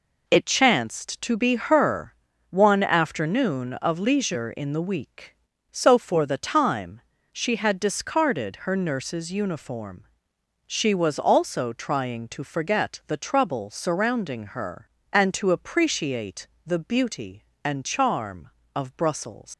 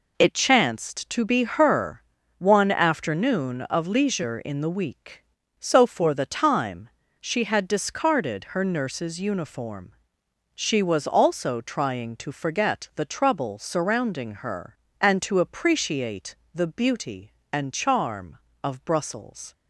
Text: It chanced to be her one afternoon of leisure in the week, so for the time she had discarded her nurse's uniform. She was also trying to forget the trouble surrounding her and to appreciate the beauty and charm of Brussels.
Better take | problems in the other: second | pauses between "her" and "one"; slight; at 2.1 s; 0.36 s long; slight in the second // pauses between "time" and "she"; slight; at 7.0 s; 0.30 s long; slight in the second // pauses between "appreciate" and "the"; slight; at 16.4 s; 0.16 s long; slight in the second // leaves "Brussels" unfinished; at 19.5 s; 105 ms

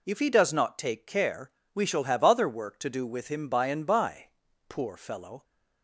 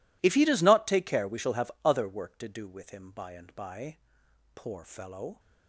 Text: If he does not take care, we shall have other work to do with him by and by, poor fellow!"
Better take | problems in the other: first | gets quieter; strong; throughout; 20.5 dB

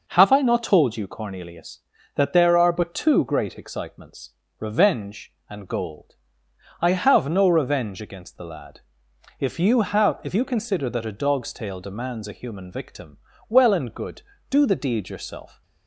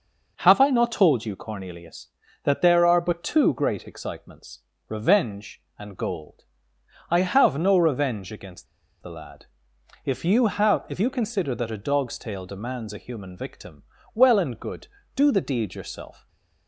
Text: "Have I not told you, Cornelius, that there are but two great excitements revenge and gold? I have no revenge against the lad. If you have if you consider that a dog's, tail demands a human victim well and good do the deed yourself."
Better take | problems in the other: first | pauses between "excitements" and "revenge"; slight; at 4.6 s; 0.28 s long; slight in the first // pauses between "against" and "the"; slight; at 8.6 s; 0.35 s long // pauses between "victim" and "well"; slight; at 13.8 s; 0.30 s long; slight in the first // stays silent after the last word; slight; from 16.1 s on; 0.5 s long

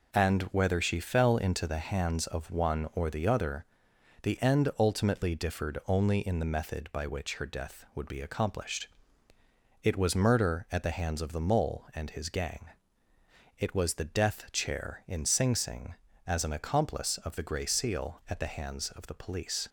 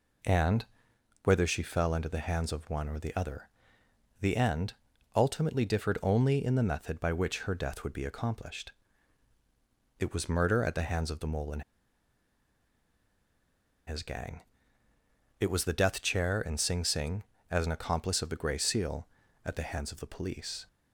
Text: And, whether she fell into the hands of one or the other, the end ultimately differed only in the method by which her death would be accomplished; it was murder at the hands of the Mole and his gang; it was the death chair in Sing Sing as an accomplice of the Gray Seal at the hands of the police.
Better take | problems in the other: first | pauses between "end" and "ultimately"; at 4.7 s; 0.42 s long // pauses between "and" and "his"; strong; at 11.6 s; 2.2 s long

